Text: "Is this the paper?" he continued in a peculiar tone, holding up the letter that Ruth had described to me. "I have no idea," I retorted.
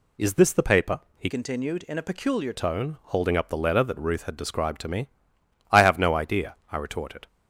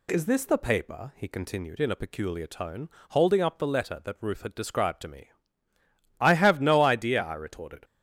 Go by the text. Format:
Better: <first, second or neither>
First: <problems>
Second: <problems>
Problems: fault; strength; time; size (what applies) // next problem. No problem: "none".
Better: second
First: changes voice from "continued" to "peculiar"; from 1.2 to 2.5 s; 1.3 s long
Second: none